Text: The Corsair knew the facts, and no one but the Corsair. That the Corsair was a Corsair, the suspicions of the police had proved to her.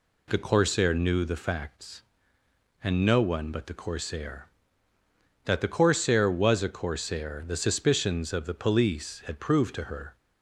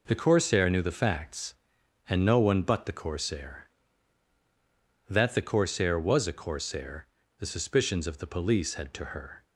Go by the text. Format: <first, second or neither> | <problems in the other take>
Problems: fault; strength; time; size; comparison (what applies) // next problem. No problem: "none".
first | skips "proved"; at 8.9 s